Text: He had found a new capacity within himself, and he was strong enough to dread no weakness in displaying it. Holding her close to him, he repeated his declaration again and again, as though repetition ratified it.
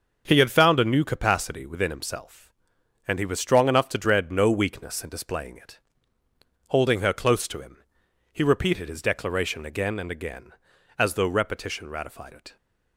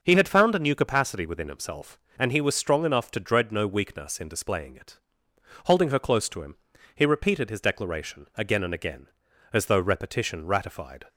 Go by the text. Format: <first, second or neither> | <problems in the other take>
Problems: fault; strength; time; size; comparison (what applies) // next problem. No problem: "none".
first | starts louder than the rest; until 1.0 s; 6 dB; also in the first // stops before "it"; at 11.0 s